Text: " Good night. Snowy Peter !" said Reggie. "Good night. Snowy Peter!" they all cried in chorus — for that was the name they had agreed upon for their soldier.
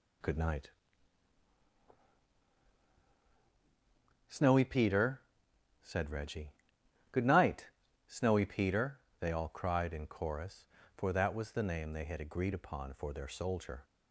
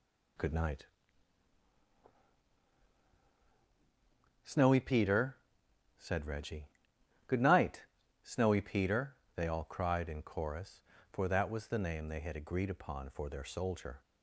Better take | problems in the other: neither | none

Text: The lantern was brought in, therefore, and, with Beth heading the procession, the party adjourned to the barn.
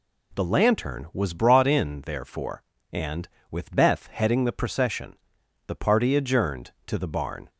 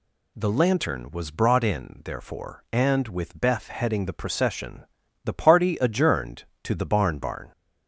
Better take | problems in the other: first | says "barn" twice; at 7.1 s

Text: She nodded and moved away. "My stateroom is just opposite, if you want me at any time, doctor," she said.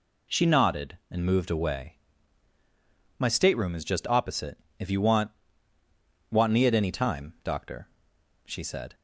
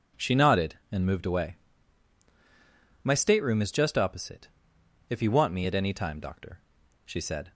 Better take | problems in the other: second | says "want" twice; at 6.3 s

